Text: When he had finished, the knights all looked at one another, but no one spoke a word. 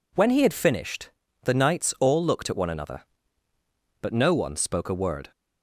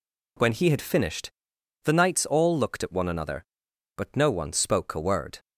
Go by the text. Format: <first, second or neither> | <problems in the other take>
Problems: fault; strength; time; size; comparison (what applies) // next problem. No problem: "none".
neither | none